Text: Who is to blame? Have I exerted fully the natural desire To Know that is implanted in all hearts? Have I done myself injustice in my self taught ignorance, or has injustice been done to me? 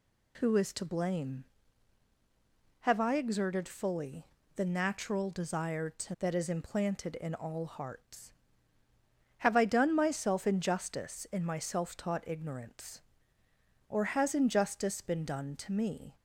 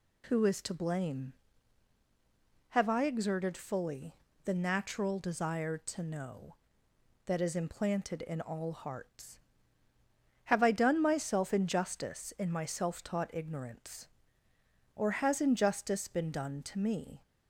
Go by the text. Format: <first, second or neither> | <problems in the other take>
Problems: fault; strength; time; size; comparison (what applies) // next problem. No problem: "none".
second | pauses between "fully" and "the"; slight; at 4.2 s; 0.30 s long; slight in the second // skips "Know"; at 6.1 s